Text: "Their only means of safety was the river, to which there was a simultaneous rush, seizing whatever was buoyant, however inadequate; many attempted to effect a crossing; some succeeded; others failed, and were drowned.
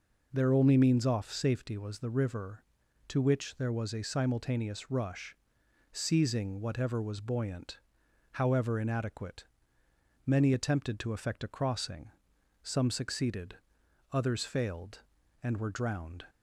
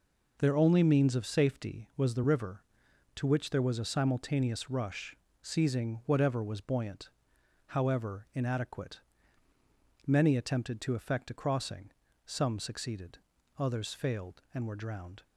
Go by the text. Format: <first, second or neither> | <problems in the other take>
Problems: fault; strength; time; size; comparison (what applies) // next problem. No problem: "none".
second | says "off" for "of"; at 1.0 s